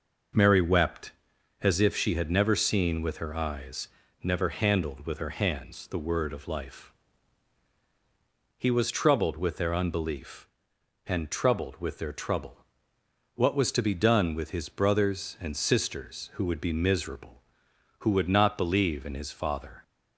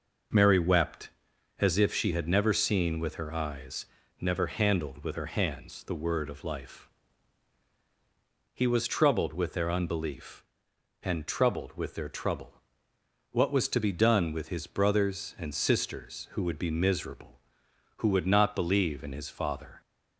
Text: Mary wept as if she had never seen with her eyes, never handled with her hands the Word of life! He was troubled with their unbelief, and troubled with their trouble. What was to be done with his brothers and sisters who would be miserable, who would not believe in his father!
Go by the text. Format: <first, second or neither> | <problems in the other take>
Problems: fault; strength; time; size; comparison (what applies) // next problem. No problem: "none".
neither | none